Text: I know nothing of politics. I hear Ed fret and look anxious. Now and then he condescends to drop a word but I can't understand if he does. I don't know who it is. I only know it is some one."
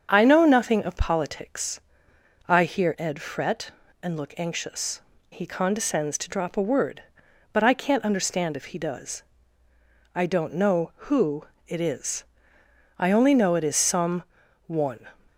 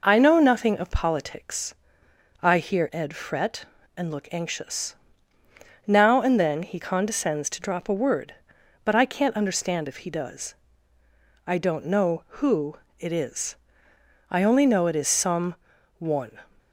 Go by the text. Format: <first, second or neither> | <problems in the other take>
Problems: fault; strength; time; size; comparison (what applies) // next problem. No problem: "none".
second | starts louder than the rest; strong; until 1.1 s; 7.5 dB // skips "Now and then"; at 5.1 s // pauses between "who" and "it"; slight; at 11.4 s; 0.24 s long; slight in the second // pauses between "some" and "one"; at 14.2 s; 0.44 s long; also in the second